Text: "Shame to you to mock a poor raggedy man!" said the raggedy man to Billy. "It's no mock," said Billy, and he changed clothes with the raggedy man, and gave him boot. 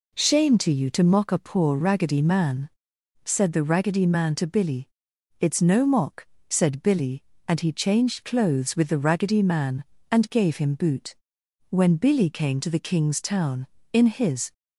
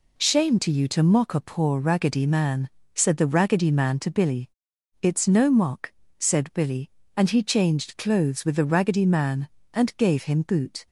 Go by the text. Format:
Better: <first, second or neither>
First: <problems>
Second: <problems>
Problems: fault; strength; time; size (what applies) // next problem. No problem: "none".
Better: second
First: goes on to say "When Billy came to the king's town in his"; strong; from 11.7 s on; 2.8 s long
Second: none